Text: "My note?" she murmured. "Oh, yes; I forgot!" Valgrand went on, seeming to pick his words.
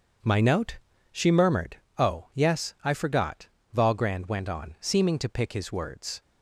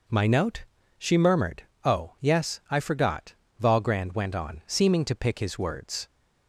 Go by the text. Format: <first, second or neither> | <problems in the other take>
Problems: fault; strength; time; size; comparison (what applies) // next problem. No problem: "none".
second | gets quieter; strong; throughout; 9 dB